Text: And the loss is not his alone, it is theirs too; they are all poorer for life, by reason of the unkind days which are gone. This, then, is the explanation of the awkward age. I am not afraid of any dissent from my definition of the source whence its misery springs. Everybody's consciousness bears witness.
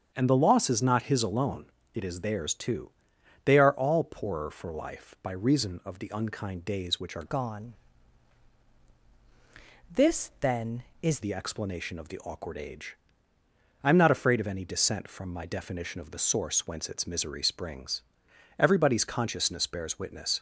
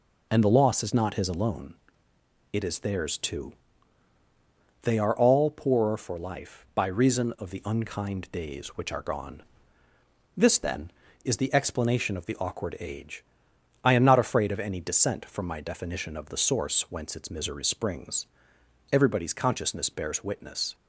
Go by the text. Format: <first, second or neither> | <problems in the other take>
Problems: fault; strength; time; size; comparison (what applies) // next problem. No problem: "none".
second | starts louder than the rest; strong; until 1.1 s; 7.5 dB // changes voice from "gone" to "is"; from 7.2 to 11.2 s; 4.0 s long